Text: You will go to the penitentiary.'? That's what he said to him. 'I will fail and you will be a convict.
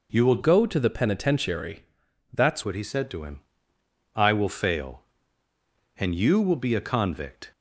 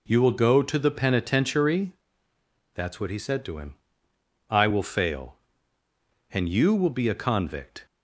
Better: second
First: changes voice from "go" to "That's"; from 0.4 to 2.6 s; 2.2 s long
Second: none

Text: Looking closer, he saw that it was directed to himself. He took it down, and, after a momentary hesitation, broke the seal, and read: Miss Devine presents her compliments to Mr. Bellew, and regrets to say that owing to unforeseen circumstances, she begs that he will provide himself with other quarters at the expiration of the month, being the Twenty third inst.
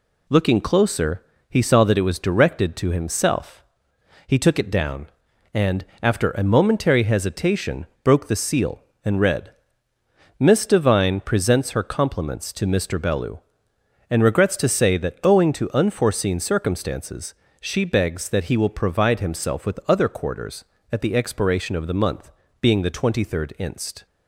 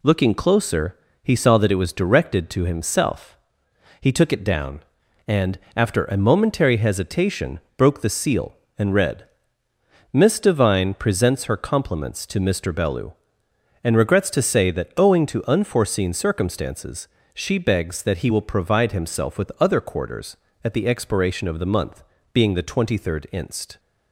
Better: neither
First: none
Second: none

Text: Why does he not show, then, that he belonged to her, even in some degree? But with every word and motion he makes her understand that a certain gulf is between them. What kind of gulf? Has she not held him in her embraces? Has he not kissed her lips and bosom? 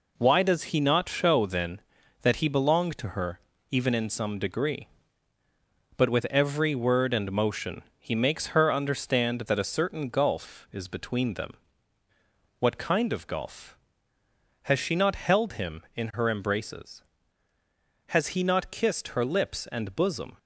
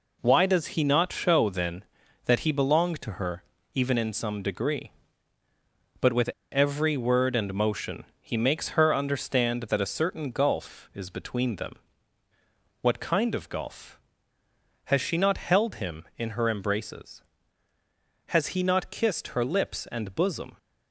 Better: first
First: pauses between "motion" and "he"; slight; at 7.8 s; 0.16 s long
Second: pauses between "with" and "every"; slight; at 6.2 s; 0.23 s long // pauses between "motion" and "he"; slight; at 8.0 s; 0.16 s long

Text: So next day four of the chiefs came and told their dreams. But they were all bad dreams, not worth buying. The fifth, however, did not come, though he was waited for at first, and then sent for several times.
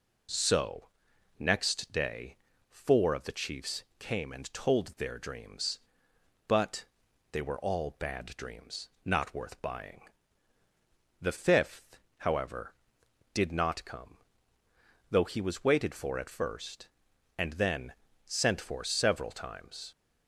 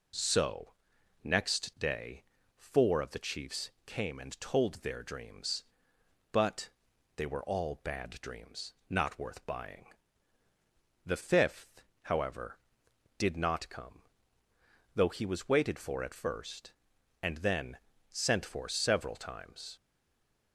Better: first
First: pauses between "So" and "next"; noticeable; at 0.8 s; 0.50 s long // pauses between "day" and "four"; slight; at 2.3 s; 0.34 s long // pauses between "chiefs" and "came"; slight; at 3.8 s; 0.16 s long // pauses between "But" and "they"; noticeable; at 6.8 s; 0.46 s long // pauses between "then" and "sent"; slight; at 17.9 s; 0.32 s long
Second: pauses between "So" and "next"; noticeable; at 0.7 s; 0.50 s long // pauses between "day" and "four"; slight; at 2.2 s; 0.34 s long // pauses between "chiefs" and "came"; slight; at 3.6 s; 0.16 s long // pauses between "But" and "they"; noticeable; at 6.7 s; 0.46 s long // pauses between "then" and "sent"; slight; at 17.7 s; 0.32 s long // stays silent after the last word; slight; from 19.7 s on; 0.8 s long

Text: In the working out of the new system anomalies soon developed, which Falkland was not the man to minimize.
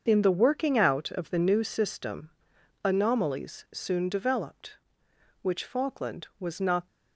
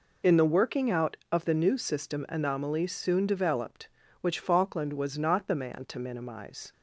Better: second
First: starts louder than the rest; until 1.0 s; 6.5 dB // pauses between "system" and "anomalies"; noticeable; at 2.2 s; 0.56 s long // stops before "the man to minimize"; at 6.8 s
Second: none

